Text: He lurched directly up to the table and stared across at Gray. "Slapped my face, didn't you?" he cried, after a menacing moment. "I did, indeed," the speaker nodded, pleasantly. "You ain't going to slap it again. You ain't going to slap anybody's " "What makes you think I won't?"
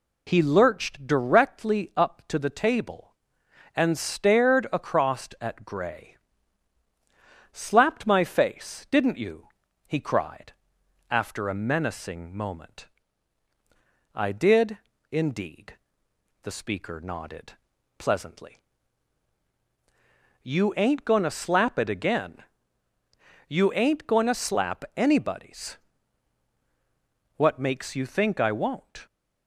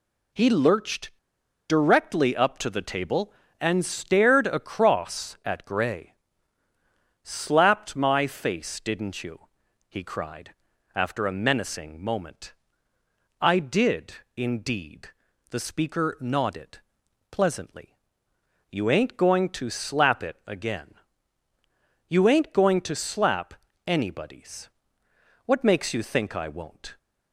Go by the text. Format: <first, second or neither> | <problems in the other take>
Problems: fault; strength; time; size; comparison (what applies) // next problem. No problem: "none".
first | pauses between "lurched" and "directly"; noticeable; at 1.1 s; 0.53 s long // pauses between "slap" and "anybody's"; slight; at 23.5 s; 0.34 s long